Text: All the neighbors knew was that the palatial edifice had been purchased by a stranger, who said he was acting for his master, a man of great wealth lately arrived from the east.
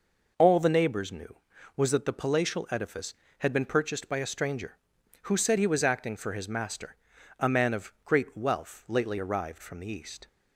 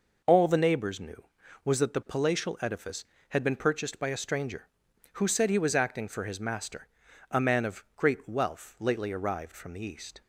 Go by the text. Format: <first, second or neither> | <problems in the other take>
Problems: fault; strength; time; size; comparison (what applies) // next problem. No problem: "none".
neither | none